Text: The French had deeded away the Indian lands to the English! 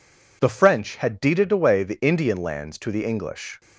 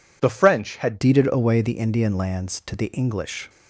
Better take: first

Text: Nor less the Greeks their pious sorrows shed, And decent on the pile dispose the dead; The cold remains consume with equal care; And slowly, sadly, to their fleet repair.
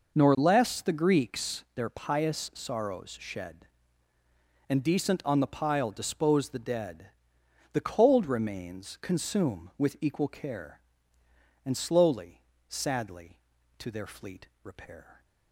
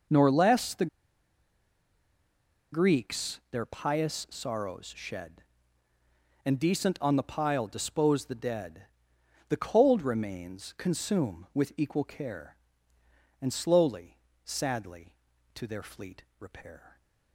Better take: first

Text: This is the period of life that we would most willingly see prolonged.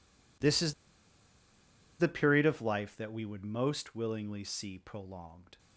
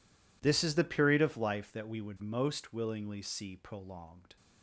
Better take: second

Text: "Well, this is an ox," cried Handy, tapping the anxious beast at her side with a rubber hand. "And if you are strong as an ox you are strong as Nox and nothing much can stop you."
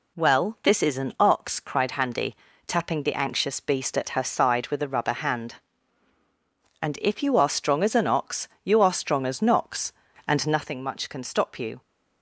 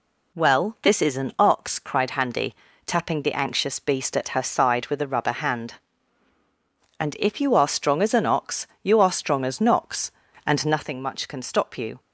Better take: neither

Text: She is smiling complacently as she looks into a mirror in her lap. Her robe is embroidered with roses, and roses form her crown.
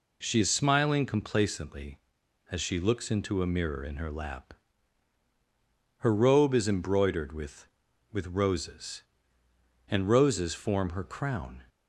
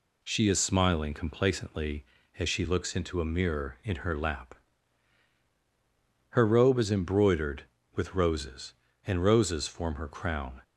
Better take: second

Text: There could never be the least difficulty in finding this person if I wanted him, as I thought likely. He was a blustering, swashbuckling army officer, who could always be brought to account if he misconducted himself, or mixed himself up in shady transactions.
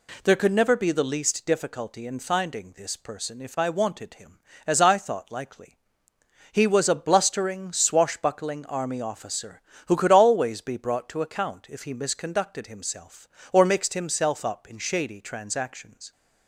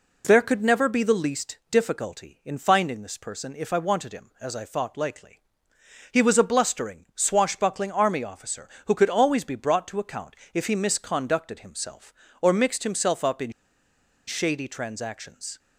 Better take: first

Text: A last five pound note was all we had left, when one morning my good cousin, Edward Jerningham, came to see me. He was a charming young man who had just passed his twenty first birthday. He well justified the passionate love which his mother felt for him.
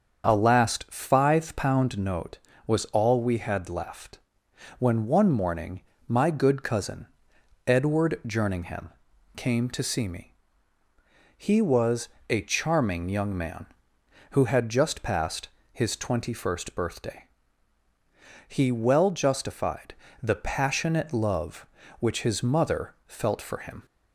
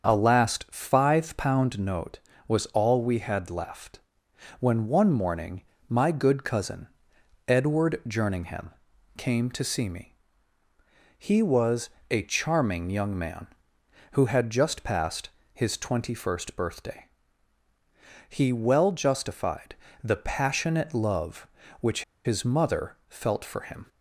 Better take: first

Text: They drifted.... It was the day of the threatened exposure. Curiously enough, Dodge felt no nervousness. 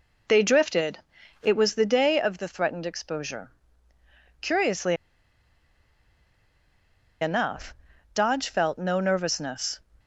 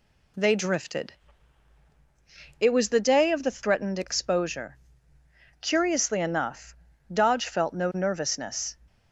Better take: second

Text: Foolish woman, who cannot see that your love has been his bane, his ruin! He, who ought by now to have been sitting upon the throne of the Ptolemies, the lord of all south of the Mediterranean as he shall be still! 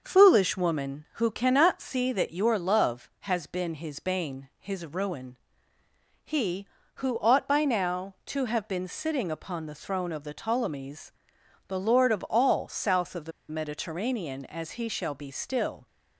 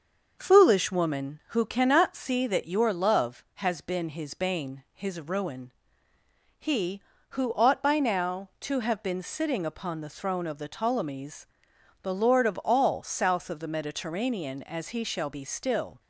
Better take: second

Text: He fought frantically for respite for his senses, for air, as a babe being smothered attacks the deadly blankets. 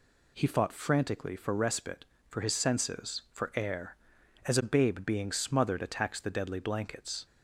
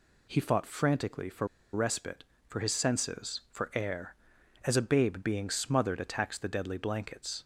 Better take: first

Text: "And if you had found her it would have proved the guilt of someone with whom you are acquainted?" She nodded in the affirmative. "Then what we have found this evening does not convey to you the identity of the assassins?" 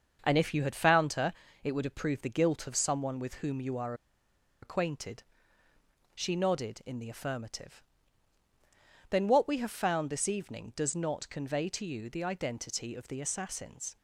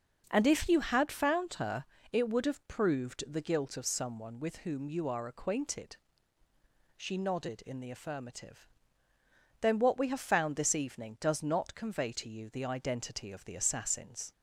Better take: second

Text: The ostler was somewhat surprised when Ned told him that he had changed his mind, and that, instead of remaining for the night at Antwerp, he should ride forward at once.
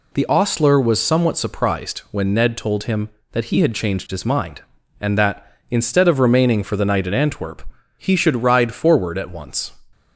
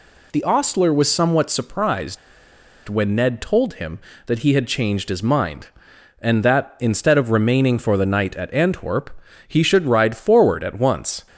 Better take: first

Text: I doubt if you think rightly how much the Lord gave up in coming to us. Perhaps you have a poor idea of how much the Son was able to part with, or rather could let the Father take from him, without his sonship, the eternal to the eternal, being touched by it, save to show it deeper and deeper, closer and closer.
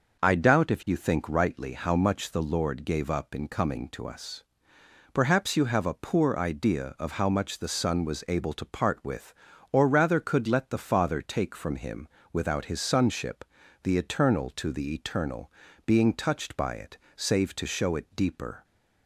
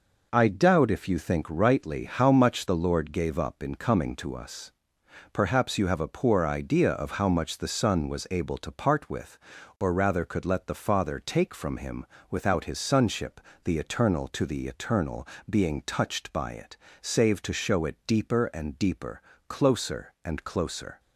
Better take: second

